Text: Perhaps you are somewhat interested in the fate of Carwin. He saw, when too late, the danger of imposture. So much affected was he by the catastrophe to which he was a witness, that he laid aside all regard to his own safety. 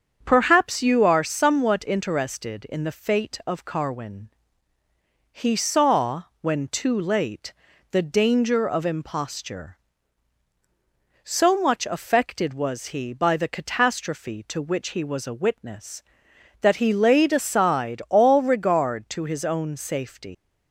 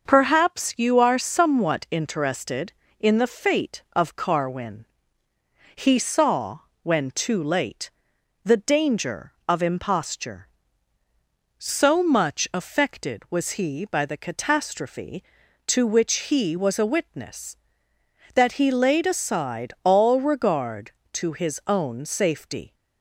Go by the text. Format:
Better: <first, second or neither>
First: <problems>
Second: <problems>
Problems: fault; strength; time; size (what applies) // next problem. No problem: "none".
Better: second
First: starts louder than the rest; strong; until 1.2 s; 7.5 dB // leaves "safety" unfinished; at 20.3 s; 110 ms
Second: starts louder than the rest; noticeable; until 1.0 s; 6 dB